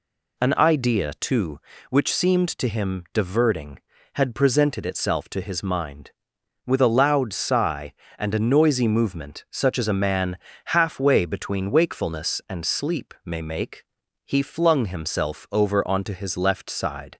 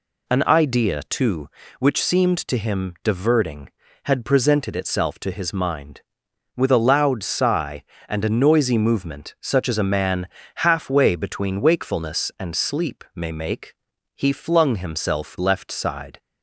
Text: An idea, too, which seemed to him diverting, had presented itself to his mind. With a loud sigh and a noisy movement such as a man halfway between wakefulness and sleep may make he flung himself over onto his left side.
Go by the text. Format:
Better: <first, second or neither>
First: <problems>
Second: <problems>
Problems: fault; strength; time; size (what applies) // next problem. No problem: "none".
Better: first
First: pauses between "man" and "halfway"; slight; at 10.3 s; 0.30 s long // pauses between "make" and "he"; at 13.8 s; 0.44 s long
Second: pauses between "man" and "halfway"; slight; at 10.2 s; 0.30 s long // pauses between "make" and "he"; at 13.7 s; 0.44 s long // skips "over onto his"; at 15.3 s